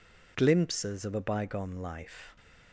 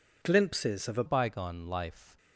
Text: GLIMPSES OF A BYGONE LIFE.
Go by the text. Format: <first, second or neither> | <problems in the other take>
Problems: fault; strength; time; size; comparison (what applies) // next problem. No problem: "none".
first | changes voice at "BYGONE"; from 1.0 s on; 1.1 s long